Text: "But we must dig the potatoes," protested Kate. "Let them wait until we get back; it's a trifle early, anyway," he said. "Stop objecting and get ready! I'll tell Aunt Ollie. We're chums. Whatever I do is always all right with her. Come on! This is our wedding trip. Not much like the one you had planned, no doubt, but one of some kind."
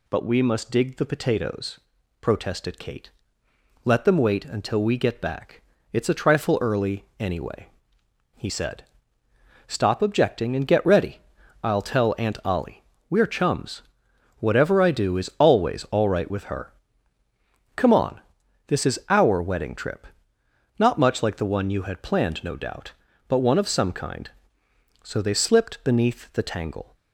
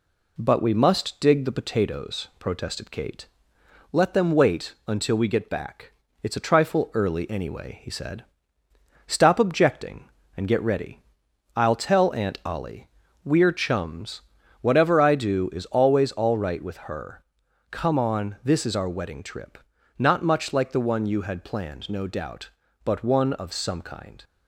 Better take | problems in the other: second | goes on to say "So they slipped beneath the tangle"; strong; from 25.0 s on; 1.9 s long

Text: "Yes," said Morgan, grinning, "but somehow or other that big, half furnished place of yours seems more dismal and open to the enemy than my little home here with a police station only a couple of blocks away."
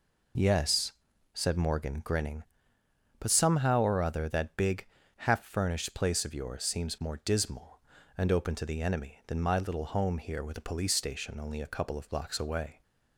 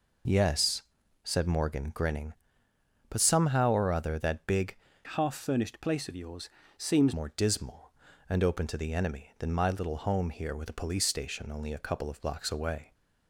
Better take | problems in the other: first | changes voice from "half" to "seems"; from 5.0 to 7.1 s; 2.1 s long // pauses between "yours" and "seems"; slight; at 6.4 s; 0.30 s long

